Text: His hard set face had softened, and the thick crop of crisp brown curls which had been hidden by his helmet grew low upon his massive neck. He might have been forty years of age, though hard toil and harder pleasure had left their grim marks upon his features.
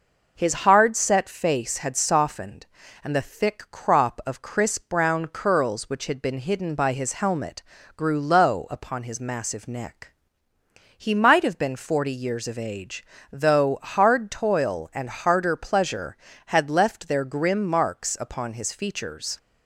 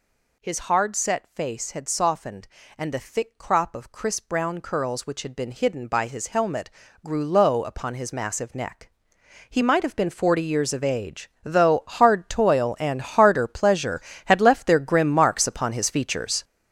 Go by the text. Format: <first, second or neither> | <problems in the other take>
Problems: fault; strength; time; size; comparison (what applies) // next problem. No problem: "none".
first | gets louder; strong; throughout; 10 dB // pauses between "helmet" and "grew"; slight; at 6.7 s; 0.34 s long; slight in the first